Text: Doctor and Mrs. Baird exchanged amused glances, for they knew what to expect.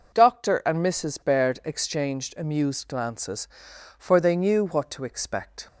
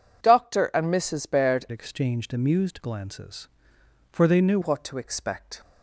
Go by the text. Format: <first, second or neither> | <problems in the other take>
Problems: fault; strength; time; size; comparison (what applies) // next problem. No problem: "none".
first | changes voice from "exchanged" to "knew"; from 1.7 to 4.5 s; 2.8 s long